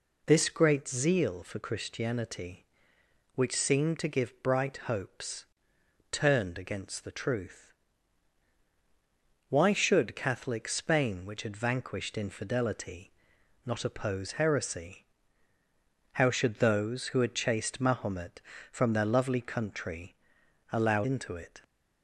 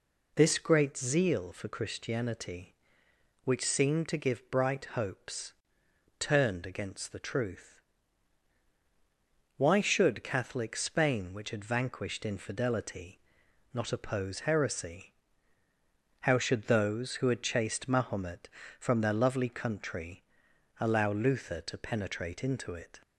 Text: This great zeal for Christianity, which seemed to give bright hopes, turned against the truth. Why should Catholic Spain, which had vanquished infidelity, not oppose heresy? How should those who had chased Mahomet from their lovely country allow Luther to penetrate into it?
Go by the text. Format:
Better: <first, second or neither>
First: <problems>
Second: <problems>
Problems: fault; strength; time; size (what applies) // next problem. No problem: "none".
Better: second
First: pauses between "country" and "allow"; noticeable; at 20.1 s; 0.56 s long // skips "Luther to penetrate"; at 21.0 s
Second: pauses between "country" and "allow"; noticeable; at 20.2 s; 0.56 s long